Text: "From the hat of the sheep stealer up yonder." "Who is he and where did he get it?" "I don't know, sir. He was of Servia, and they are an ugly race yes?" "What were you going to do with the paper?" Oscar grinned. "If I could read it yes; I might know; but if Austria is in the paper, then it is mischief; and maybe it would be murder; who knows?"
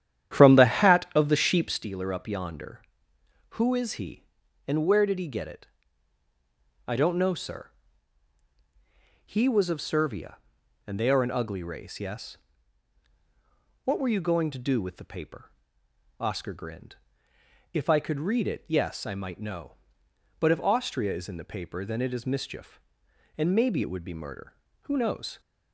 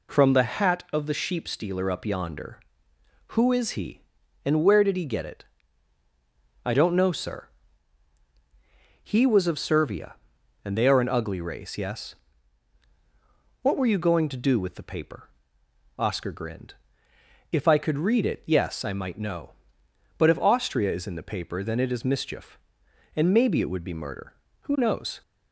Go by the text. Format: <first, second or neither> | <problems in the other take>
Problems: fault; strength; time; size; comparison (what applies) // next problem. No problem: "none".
second | starts louder than the rest; strong; until 1.9 s; 10.5 dB